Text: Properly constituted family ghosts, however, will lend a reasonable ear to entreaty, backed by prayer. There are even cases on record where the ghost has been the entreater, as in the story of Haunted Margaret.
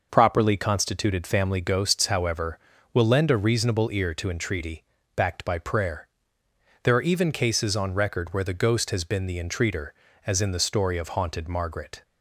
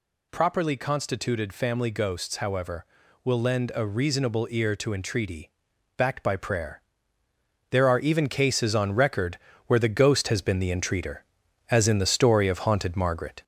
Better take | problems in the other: first | gets louder; slight; throughout; 3 dB // pauses between "record" and "where"; slight; at 9.3 s; 0.30 s long

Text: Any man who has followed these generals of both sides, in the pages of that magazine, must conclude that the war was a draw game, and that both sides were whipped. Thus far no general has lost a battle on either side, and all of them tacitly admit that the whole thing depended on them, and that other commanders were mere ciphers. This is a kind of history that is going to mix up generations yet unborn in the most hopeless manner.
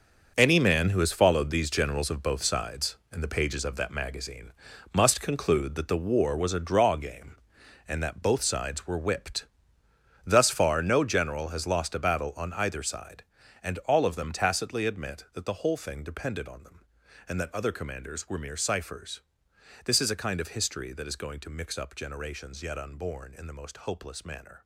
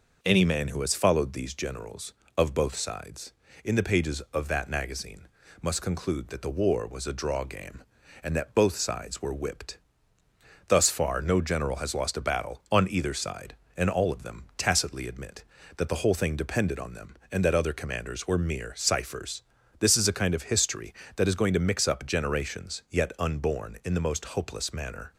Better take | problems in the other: second | gets quieter; strong; throughout; 11 dB

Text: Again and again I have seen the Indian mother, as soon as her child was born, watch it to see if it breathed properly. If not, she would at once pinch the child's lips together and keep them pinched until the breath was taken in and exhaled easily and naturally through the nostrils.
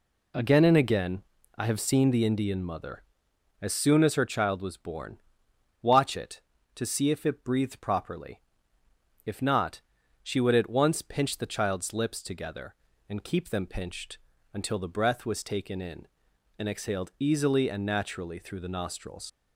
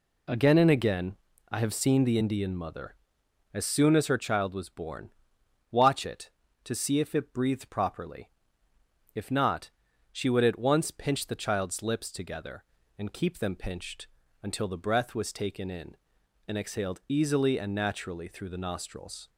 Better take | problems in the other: second | pauses between "again" and "I"; slight; at 1.2 s; 0.34 s long; slight in the second // pauses between "pinched" and "until"; slight; at 14.1 s; 0.36 s long; slight in the second // leaves "nostrils" unfinished; at 19.2 s; 100 ms

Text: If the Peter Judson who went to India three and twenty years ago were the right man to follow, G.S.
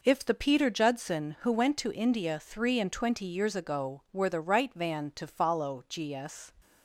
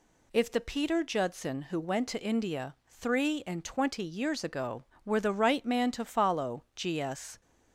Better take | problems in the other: second | says "van" for "man"; at 4.7 s

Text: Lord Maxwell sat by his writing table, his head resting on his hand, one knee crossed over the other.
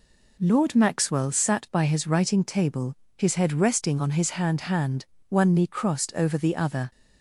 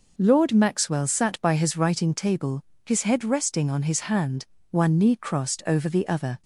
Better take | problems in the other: second | says "hand" twice; at 4.6 s

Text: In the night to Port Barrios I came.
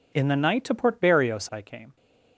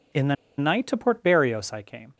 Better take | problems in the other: first | pauses between "the" and "night"; slight; at 0.3 s; 0.23 s long

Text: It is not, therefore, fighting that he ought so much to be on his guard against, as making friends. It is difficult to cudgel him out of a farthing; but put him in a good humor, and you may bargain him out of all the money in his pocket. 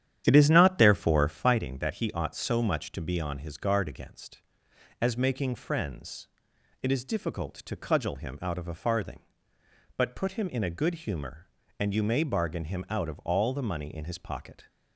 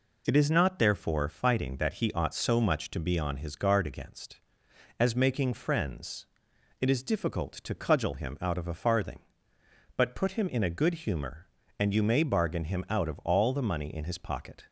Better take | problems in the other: second | starts louder than the rest; strong; until 1.7 s; 10 dB

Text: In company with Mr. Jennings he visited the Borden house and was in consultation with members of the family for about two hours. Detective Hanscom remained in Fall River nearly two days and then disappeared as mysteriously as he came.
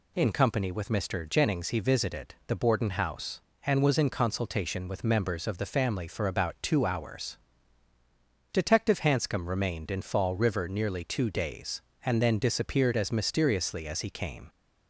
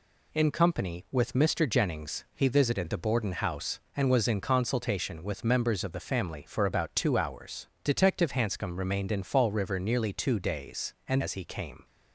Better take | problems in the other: first | skips "then disappeared as mysteriously"; at 11.2 s

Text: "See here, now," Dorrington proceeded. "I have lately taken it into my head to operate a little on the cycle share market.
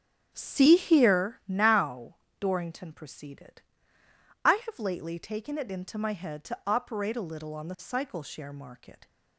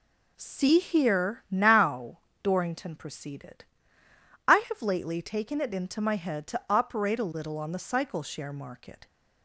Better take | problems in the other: second | starts louder than the rest; strong; until 1.3 s; 9 dB

